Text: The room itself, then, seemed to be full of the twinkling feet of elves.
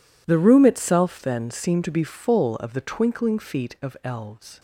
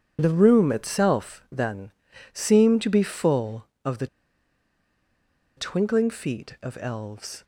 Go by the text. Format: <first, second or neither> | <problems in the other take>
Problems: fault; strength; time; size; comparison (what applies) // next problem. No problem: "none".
first | pauses between "the" and "twinkling"; strong; at 4.0 s; 1.5 s long